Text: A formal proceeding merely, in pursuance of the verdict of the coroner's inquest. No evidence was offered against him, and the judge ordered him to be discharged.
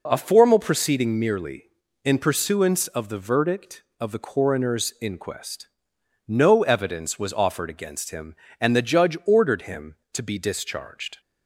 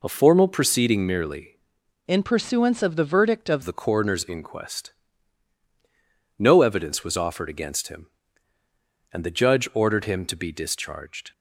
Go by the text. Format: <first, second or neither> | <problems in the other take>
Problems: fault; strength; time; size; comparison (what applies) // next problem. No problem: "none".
first | changes voice from "in" to "of"; from 2.0 to 3.6 s; 1.6 s long